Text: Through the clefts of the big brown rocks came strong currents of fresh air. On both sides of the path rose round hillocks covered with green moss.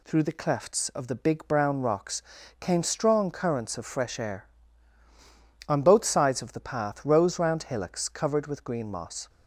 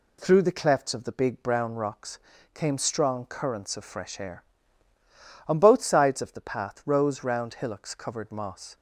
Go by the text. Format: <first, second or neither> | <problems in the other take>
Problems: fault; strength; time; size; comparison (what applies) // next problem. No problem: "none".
first | pauses between "rocks" and "came"; slight; at 2.1 s; 0.34 s long; slight in the first // skips "with green"; at 8.2 s